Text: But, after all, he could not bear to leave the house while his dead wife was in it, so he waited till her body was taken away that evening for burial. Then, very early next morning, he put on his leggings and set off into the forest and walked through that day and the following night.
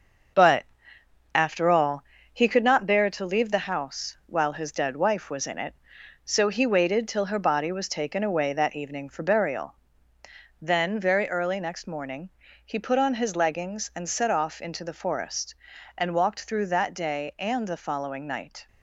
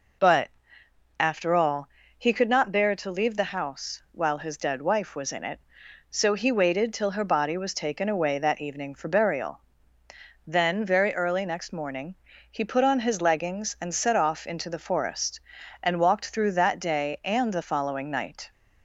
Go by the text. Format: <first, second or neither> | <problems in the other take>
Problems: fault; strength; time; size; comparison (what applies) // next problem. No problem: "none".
second | gets quieter; noticeable; throughout; 6 dB